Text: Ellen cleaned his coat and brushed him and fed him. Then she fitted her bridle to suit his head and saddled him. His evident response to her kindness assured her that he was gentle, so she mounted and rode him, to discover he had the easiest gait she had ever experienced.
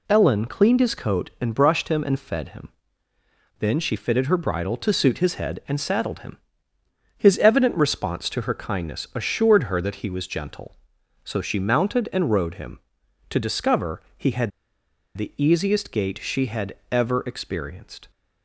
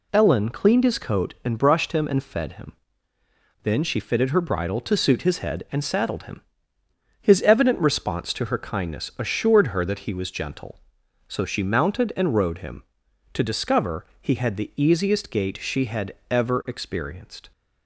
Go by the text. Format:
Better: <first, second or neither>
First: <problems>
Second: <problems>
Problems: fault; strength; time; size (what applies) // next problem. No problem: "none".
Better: second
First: pauses between "had" and "the"; noticeable; at 14.5 s; 0.67 s long // pauses between "had" and "ever"; slight; at 16.7 s; 0.16 s long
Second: pauses between "had" and "ever"; slight; at 16.1 s; 0.16 s long